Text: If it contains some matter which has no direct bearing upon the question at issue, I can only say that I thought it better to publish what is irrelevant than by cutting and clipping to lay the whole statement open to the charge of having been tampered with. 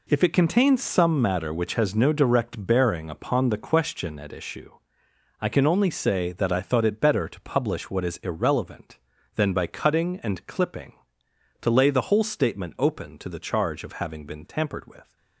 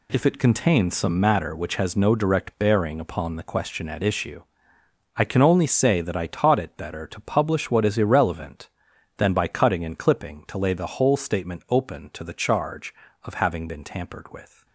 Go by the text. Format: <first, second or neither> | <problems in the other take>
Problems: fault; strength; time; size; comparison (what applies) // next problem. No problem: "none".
first | says "taught" for "thought"; at 6.2 s